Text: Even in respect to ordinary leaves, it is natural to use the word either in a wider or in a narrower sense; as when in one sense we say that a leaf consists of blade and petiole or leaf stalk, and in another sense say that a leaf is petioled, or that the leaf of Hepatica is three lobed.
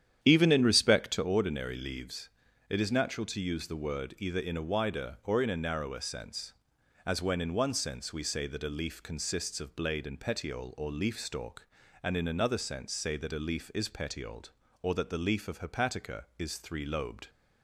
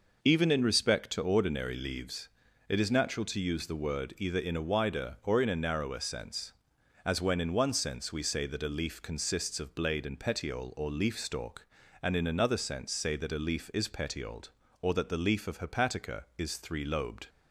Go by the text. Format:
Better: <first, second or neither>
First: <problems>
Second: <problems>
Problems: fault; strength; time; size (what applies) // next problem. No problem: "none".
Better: second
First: starts louder than the rest; strong; until 1.3 s; 9.5 dB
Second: none